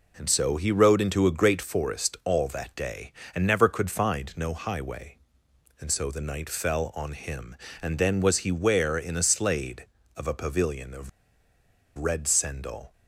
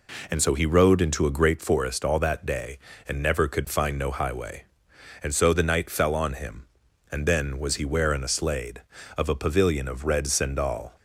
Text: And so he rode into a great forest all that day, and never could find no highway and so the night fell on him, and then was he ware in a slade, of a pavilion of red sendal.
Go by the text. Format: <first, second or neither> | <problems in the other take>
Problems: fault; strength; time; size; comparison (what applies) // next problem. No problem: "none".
second | pauses between "of" and "red"; noticeable; at 11.0 s; 0.88 s long